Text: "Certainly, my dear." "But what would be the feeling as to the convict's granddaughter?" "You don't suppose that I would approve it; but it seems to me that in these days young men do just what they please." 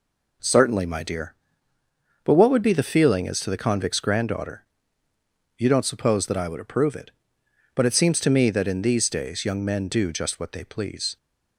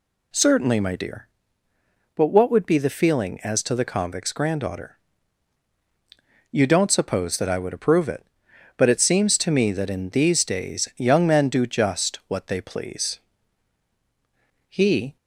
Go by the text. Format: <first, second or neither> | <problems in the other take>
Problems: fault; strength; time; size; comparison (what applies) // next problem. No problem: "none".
first | goes on to say "He"; slight; from 14.7 s on; 0.46 s long